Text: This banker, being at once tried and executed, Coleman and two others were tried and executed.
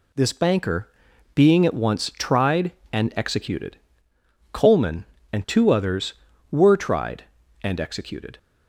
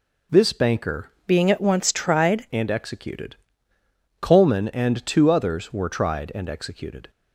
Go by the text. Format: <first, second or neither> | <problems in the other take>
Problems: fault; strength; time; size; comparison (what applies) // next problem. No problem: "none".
first | changes voice from "being" to "tried"; from 1.2 to 2.4 s; 1.2 s long